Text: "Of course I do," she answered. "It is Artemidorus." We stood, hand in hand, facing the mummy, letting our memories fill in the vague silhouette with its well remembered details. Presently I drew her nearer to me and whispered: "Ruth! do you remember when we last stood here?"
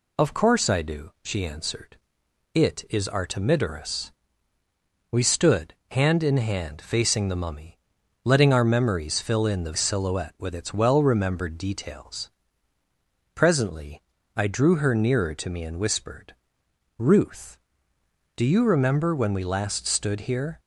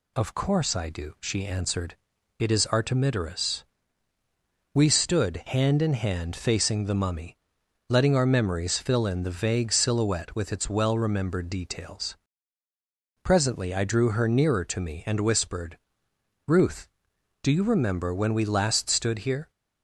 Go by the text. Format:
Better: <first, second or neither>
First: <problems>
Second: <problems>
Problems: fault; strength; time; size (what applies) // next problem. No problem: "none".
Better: second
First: skips "vague"; at 9.7 s // pauses between "Presently" and "I"; slight; at 14.0 s; 0.32 s long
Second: none